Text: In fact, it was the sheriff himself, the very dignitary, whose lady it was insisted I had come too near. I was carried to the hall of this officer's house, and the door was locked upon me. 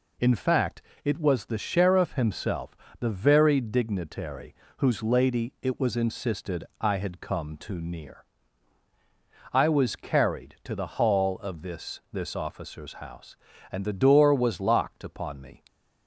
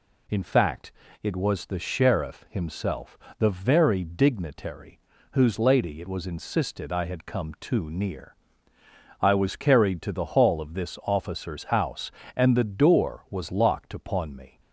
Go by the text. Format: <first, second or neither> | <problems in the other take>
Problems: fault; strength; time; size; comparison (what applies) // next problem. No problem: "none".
second | pauses between "insisted" and "I"; slight; at 6.6 s; 0.18 s long // says "this" twice; at 12.1 s